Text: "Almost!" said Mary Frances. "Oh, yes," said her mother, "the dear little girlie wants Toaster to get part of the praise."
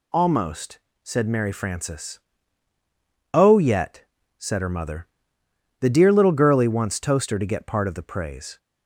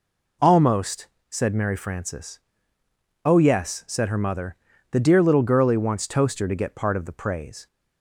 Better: second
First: says "yet" for "yes"; at 3.5 s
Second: none

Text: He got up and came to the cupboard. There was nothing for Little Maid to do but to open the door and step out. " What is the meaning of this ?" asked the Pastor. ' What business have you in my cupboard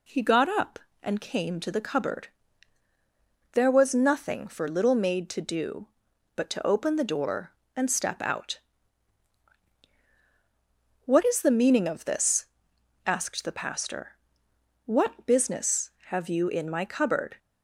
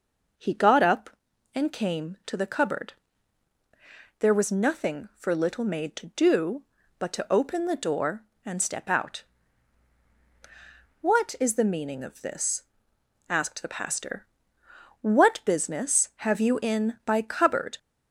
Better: first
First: none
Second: says "by" for "my"; at 17.0 s

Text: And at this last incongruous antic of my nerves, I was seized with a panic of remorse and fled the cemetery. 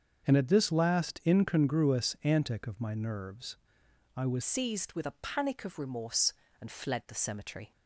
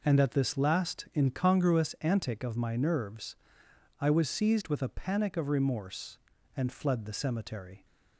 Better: second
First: starts louder than the rest; until 1.3 s; 7 dB // changes voice at "seized"; from 4.4 s on; 3.3 s long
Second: none

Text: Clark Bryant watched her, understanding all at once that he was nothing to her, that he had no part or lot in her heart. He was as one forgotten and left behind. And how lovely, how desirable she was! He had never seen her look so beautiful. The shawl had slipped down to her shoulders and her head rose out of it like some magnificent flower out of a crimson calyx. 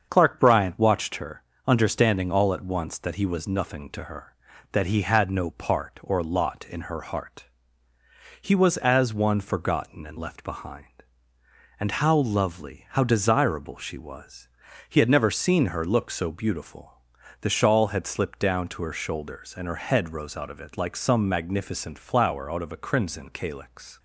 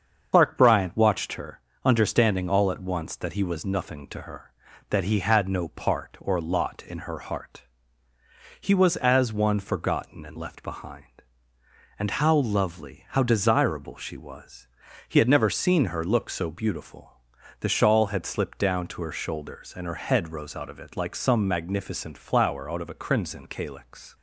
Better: first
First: starts louder than the rest; until 1.1 s; 7 dB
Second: loses the start of "Clark"; at 0.3 s; 50 ms // starts louder than the rest; until 1.3 s; 7 dB

